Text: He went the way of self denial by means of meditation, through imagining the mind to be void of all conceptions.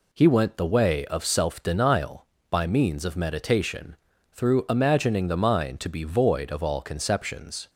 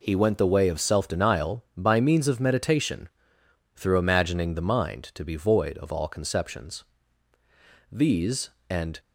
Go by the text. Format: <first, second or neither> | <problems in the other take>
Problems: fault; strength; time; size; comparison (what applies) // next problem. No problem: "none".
first | goes on to say "These and"; noticeable; from 7.9 s on; 1.0 s long